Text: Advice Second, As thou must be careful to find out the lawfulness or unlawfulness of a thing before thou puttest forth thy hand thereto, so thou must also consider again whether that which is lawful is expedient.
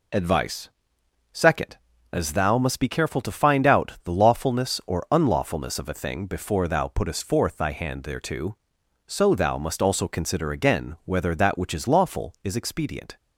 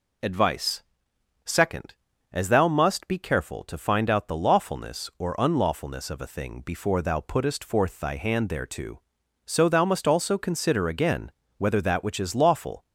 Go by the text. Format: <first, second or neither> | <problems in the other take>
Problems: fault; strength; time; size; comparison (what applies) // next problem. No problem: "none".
first | pauses between "Advice" and "Second"; noticeable; at 0.8 s; 0.64 s long; noticeable in the first // pauses between "again" and "whether"; slight; at 11.3 s; 0.28 s long // stops before "is expedient"; at 12.8 s